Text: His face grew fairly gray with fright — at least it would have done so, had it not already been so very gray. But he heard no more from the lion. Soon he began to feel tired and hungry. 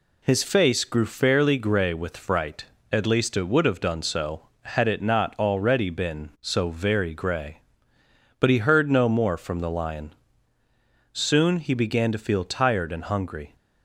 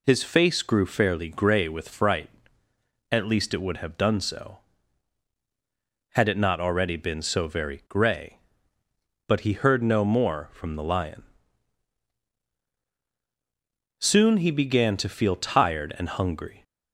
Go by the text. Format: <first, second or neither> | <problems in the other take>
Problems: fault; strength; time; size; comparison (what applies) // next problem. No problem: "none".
neither | none